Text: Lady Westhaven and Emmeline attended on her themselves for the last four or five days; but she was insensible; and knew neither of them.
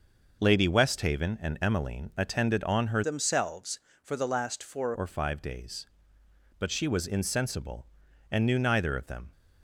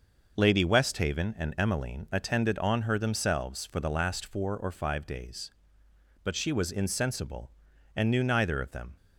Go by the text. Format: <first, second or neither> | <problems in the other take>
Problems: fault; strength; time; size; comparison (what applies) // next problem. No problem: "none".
second | changes voice from "themselves" to "four"; from 3.0 to 4.9 s; 1.9 s long